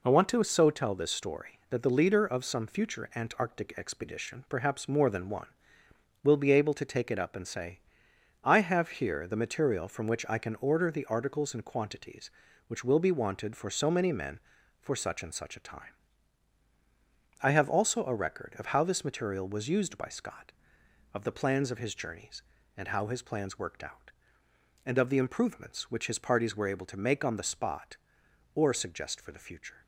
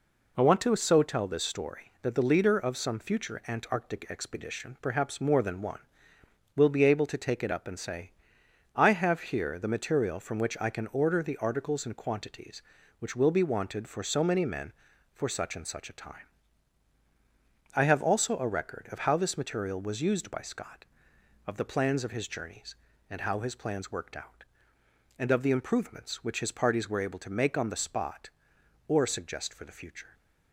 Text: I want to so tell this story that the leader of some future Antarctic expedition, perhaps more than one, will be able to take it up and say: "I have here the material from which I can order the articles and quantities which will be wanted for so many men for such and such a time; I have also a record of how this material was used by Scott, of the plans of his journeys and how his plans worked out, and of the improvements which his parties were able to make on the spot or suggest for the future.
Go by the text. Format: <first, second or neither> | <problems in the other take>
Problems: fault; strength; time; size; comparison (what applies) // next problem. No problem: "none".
neither | none